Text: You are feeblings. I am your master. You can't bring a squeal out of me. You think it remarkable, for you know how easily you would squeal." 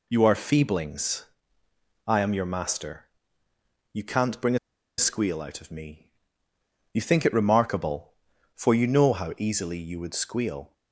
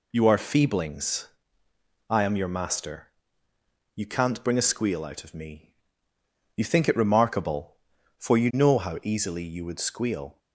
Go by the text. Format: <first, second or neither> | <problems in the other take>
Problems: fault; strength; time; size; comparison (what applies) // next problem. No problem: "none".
second | pauses between "a" and "squeal"; at 4.5 s; 0.40 s long